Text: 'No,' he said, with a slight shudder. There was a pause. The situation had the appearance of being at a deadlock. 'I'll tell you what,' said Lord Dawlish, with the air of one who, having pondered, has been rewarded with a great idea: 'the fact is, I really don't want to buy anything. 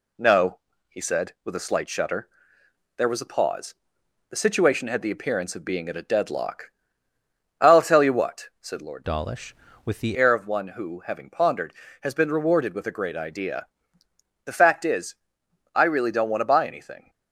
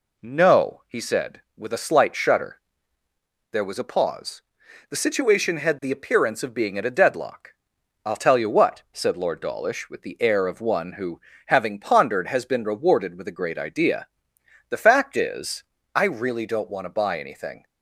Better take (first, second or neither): second